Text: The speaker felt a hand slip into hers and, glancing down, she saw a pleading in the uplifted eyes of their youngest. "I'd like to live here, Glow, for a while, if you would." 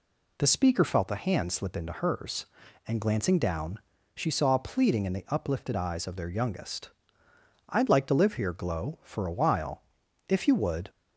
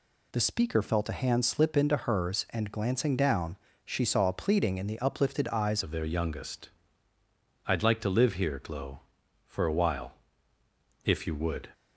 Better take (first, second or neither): first